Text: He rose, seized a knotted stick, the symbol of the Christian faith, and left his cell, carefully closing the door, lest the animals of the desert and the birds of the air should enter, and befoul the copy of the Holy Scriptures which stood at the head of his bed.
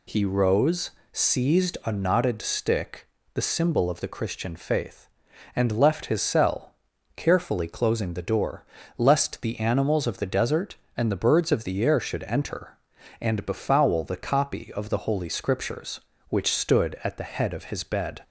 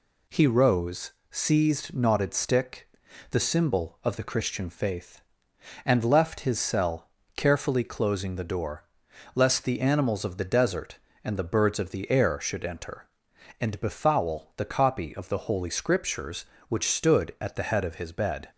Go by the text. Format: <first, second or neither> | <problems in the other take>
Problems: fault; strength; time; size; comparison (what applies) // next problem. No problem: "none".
first | skips "a"; at 1.9 s